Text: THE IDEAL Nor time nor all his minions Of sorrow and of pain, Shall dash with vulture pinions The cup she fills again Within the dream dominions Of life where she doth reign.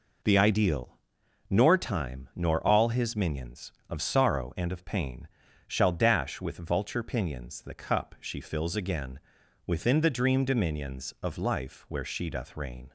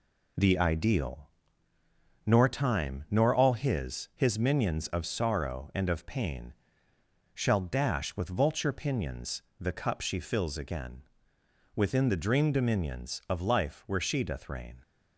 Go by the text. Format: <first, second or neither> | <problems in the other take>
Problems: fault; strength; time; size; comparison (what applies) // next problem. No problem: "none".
first | pauses between "IDEAL" and "Nor"; noticeable; at 1.2 s; 0.96 s long; noticeable in the first // says "his" twice; at 4.1 s // pauses between "pinions" and "The"; slight; at 9.3 s; 0.18 s long // pauses between "again" and "Within"; noticeable; at 11.0 s; 0.70 s long; noticeable in the first